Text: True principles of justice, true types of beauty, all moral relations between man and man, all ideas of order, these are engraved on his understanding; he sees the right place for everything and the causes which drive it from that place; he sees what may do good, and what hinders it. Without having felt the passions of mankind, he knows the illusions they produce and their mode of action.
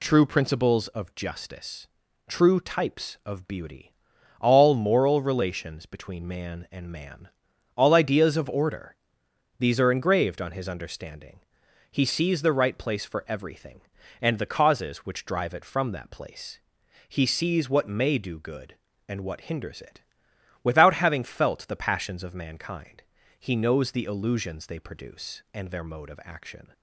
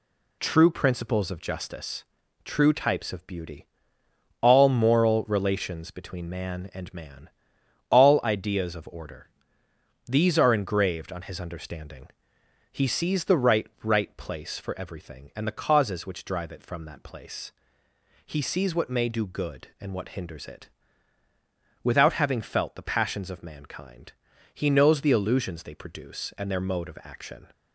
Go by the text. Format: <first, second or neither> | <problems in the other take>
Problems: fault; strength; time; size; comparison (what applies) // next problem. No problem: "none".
first | says "right" twice; at 13.8 s